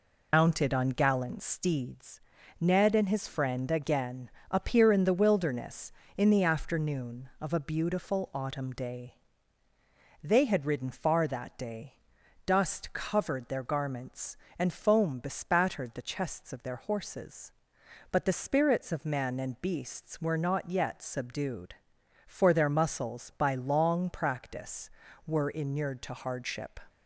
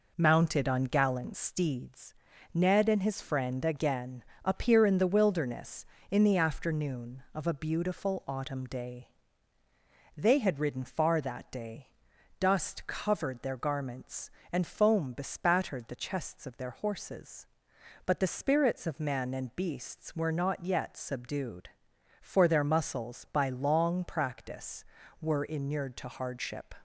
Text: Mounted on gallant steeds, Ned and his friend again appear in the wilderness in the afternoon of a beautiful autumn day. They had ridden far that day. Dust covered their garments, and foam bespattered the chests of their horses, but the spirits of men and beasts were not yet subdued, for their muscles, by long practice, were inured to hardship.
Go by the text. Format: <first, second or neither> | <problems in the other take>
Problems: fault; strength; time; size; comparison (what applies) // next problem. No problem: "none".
second | loses the start of "Mounted"; at 0.3 s; 115 ms // pauses between "again" and "appear"; slight; at 4.2 s; 0.22 s long; slight in the second